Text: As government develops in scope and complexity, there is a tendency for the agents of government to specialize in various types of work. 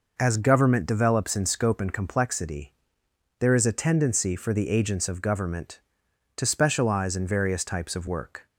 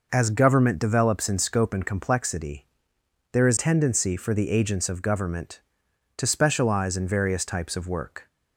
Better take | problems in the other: first | skips "a"; at 3.5 s

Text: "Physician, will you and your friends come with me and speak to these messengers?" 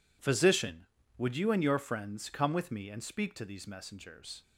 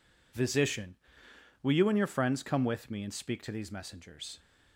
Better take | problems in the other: second | says "would" for "will"; at 1.1 s

